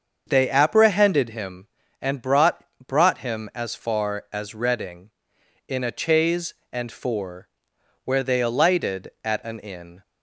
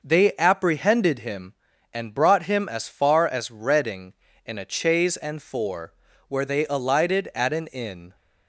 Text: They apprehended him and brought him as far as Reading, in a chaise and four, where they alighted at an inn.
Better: second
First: starts louder than the rest; until 1.2 s; 6.5 dB // says "brought" twice; at 2.8 s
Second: none

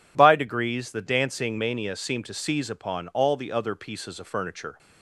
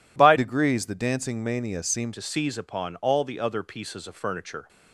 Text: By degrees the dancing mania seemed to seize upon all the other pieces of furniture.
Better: first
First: none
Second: changes voice from "degrees" to "seemed"; from 0.3 to 2.1 s; 1.8 s long

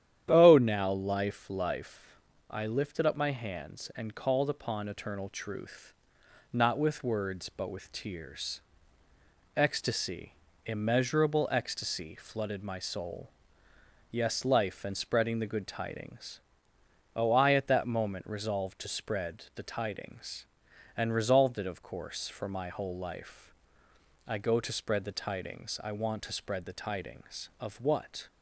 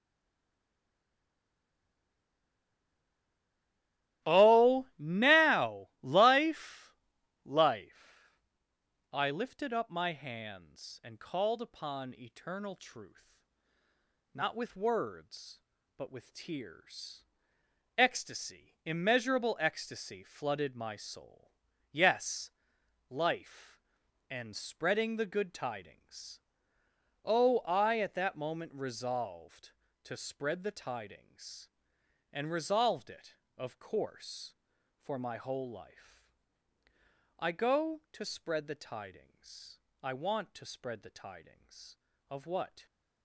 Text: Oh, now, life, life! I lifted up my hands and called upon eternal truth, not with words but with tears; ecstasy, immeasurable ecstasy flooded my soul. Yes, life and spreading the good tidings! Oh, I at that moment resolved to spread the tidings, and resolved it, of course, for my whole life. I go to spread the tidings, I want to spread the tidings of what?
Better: first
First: starts louder than the rest; strong; until 1.3 s; 10.5 dB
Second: stays silent before the first word; strong; until 4.2 s; 4.2 s long // starts louder than the rest; strong; until 5.3 s; 14.5 dB

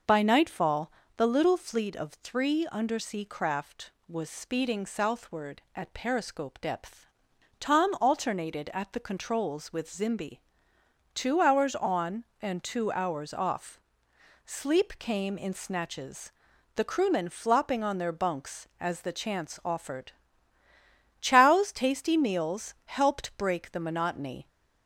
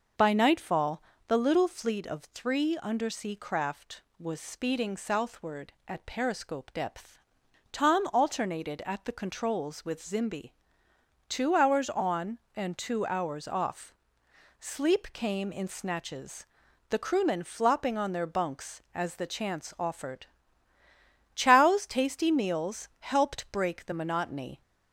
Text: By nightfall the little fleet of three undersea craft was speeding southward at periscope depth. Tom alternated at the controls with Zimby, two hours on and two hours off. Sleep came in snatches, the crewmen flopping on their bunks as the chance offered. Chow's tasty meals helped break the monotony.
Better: neither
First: pauses between "nightfall" and "the"; slight; at 0.9 s; 0.26 s long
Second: pauses between "nightfall" and "the"; slight; at 1.0 s; 0.26 s long

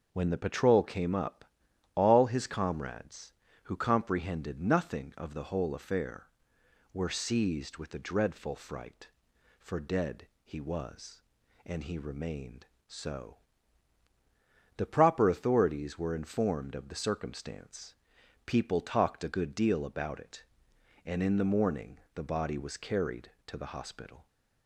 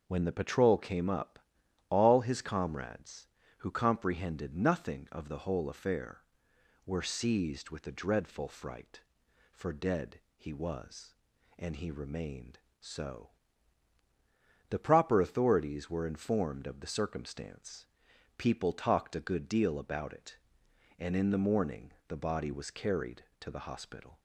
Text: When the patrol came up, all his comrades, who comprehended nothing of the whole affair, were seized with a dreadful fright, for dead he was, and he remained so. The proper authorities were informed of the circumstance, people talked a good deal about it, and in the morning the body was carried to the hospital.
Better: neither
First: starts louder than the rest; until 1.1 s; 6.5 dB // pauses between "dead" and "he"; slight; at 10.2 s; 0.16 s long // pauses between "morning" and "the"; slight; at 21.9 s; 0.16 s long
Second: starts louder than the rest; until 1.0 s; 6 dB // pauses between "dead" and "he"; slight; at 10.1 s; 0.16 s long // pauses between "morning" and "the"; slight; at 21.9 s; 0.16 s long

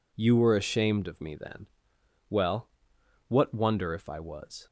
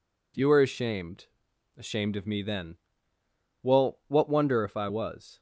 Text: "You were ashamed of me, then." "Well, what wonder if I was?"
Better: first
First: none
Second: says "ashamed" twice; at 1.7 s

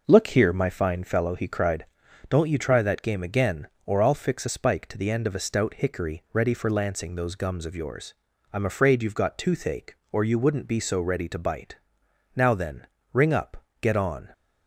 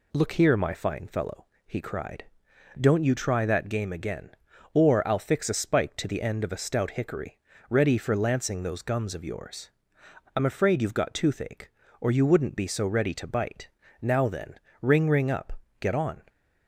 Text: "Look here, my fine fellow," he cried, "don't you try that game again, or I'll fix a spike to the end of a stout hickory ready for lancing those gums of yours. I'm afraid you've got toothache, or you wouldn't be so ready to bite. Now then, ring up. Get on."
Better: first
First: none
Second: pauses between "hickory" and "ready"; slight; at 7.3 s; 0.32 s long // says "ring" twice; at 15.1 s

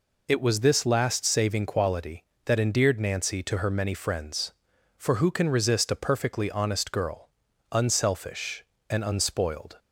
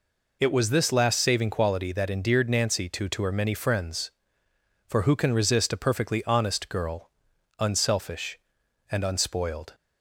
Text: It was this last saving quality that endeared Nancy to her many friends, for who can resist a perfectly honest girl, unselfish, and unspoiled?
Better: first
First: none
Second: says "to" twice; at 3.0 s

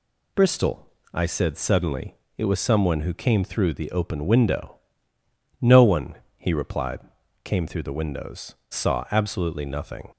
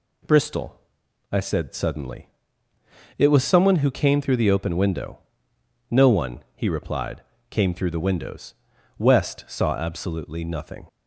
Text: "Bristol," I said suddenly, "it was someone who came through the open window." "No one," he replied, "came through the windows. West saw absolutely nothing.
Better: second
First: skips "West"; at 8.6 s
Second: none

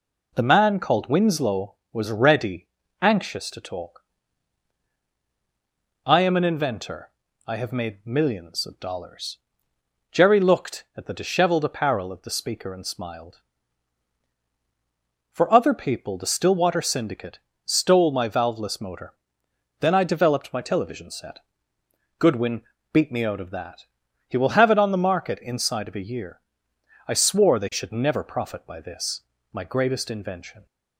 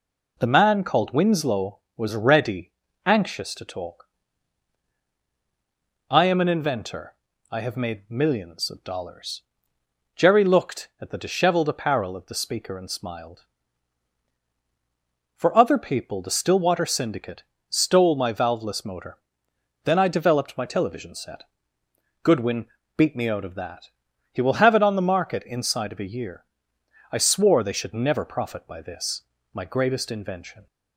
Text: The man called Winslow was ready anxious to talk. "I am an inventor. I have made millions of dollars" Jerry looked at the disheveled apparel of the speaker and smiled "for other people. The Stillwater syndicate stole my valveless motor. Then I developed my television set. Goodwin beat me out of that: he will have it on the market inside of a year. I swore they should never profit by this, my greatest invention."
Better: neither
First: pauses between "ready" and "anxious"; slight; at 2.6 s; 0.36 s long // pauses between "dollars" and "Jerry"; noticeable; at 9.3 s; 0.74 s long // pauses between "syndicate" and "stole"; slight; at 17.3 s; 0.30 s long // pauses between "Goodwin" and "beat"; slight; at 22.6 s; 0.28 s long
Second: pauses between "ready" and "anxious"; slight; at 2.7 s; 0.36 s long // pauses between "dollars" and "Jerry"; noticeable; at 9.4 s; 0.74 s long // pauses between "syndicate" and "stole"; slight; at 17.4 s; 0.30 s long // pauses between "Goodwin" and "beat"; slight; at 22.6 s; 0.28 s long

